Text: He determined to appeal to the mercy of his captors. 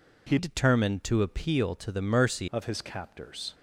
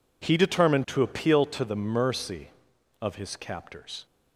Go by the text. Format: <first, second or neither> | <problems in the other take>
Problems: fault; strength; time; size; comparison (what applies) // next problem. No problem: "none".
second | changes voice from "determined" to "mercy"; from 0.3 to 2.4 s; 2.1 s long